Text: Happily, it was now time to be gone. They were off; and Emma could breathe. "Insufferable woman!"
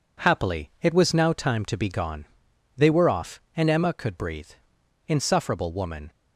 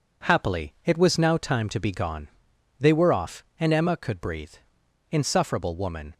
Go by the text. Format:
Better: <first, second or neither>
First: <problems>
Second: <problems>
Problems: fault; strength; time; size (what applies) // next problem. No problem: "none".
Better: neither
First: none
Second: none